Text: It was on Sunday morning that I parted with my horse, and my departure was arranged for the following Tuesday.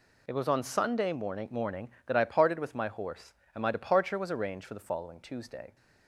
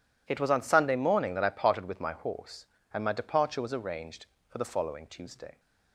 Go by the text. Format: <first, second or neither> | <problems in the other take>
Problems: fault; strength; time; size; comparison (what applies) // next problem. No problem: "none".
second | says "morning" twice; at 1.4 s